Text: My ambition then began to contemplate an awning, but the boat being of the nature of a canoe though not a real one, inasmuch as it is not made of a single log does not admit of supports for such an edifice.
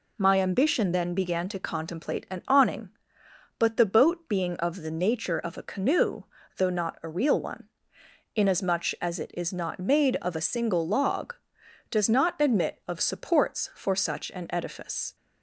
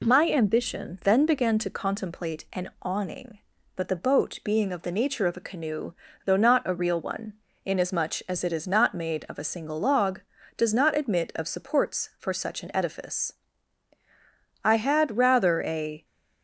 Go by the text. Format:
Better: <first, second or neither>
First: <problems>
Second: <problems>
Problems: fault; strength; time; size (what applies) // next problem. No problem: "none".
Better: first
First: pauses between "canoe" and "though"; slight; at 6.2 s; 0.34 s long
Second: pauses between "canoe" and "though"; slight; at 5.9 s; 0.32 s long // goes on to say "I had rather a"; from 14.6 s on; 1.4 s long